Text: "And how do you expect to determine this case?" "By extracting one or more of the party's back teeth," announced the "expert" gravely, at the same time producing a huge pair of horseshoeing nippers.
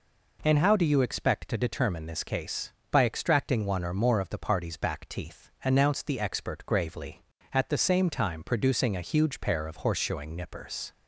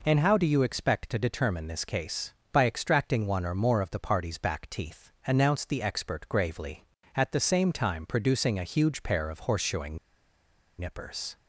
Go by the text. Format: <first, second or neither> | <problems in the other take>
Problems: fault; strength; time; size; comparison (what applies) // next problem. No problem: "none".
first | pauses between "horseshoeing" and "nippers"; noticeable; at 9.9 s; 0.81 s long